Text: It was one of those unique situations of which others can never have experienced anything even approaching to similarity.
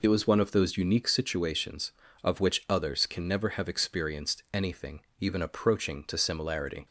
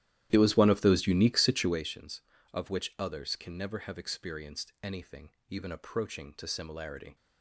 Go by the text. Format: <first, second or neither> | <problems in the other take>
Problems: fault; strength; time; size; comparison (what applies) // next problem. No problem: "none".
first | starts louder than the rest; strong; until 1.9 s; 13 dB // pauses between "anything" and "even"; slight; at 5.2 s; 0.20 s long; slight in the first